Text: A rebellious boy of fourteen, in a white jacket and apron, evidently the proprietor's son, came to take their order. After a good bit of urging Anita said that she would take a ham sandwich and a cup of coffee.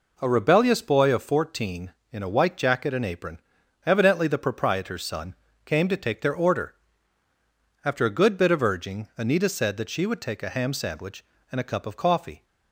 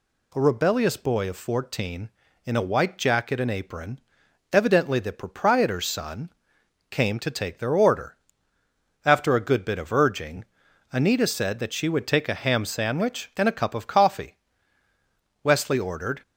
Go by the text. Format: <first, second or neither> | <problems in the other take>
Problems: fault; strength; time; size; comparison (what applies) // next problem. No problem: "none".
first | pauses between "urging" and "Anita"; noticeable; at 10.4 s; 0.50 s long // goes on to say "Wesley ordered"; noticeable; from 15.4 s on; 0.80 s long